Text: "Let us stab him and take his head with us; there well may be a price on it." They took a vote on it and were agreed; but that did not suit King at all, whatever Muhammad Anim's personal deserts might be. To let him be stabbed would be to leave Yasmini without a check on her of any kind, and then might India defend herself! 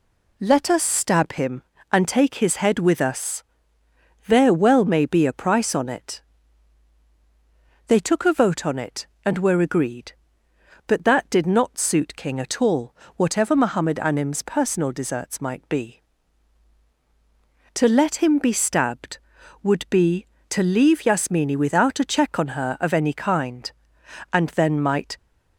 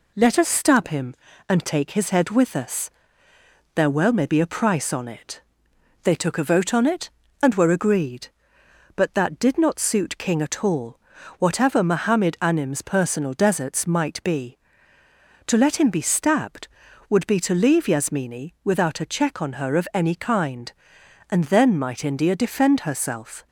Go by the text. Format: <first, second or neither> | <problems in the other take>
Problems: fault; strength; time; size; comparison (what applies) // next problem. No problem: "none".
second | stops before "India defend herself"; at 25.1 s